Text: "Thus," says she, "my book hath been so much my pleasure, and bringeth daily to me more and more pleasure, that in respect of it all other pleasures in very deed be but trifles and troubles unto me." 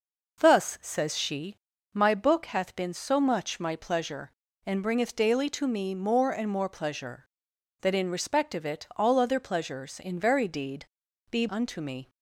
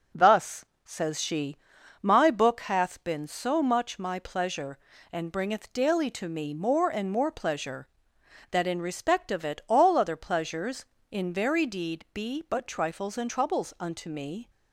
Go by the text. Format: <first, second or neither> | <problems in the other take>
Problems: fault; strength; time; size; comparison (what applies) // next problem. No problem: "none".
second | pauses between "deed" and "be"; noticeable; at 10.8 s; 0.46 s long // skips "but trifles and troubles"; at 11.4 s